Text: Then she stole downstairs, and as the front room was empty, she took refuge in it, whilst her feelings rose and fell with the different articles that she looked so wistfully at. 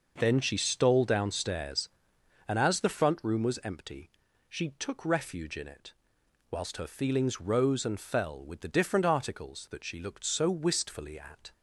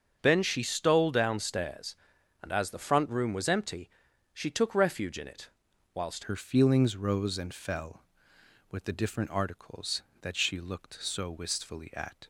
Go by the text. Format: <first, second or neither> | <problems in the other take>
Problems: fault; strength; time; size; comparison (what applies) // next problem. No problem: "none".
first | starts louder than the rest; strong; until 1.2 s; 7 dB // changes voice at "her"; from 6.2 s on; 6.0 s long